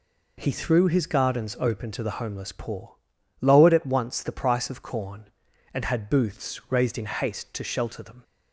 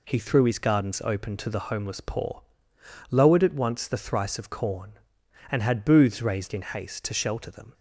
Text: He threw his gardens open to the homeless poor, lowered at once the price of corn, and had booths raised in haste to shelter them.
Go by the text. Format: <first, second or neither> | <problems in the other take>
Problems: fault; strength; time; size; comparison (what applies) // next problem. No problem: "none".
first | says "thrice" for "price"; at 3.9 s